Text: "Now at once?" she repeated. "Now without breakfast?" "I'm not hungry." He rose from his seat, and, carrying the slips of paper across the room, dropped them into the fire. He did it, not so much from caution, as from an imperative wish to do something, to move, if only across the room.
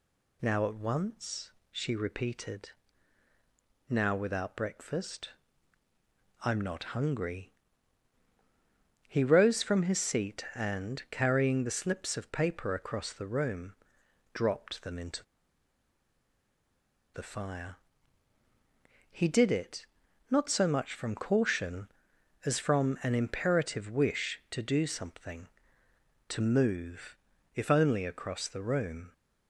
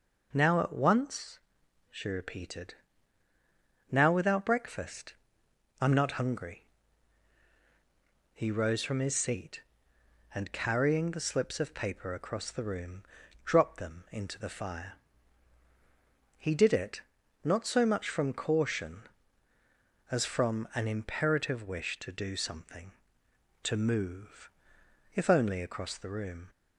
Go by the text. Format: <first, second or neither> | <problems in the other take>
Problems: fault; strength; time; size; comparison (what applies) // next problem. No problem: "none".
second | pauses between "into" and "the"; strong; at 15.2 s; 1.9 s long